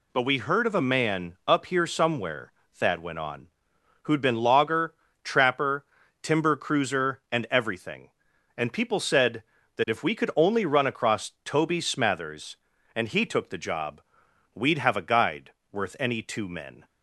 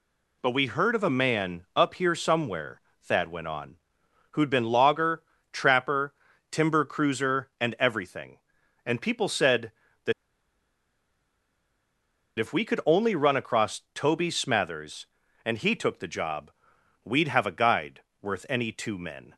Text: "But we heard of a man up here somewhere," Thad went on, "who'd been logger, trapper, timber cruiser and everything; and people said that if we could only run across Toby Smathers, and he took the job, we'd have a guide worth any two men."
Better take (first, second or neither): first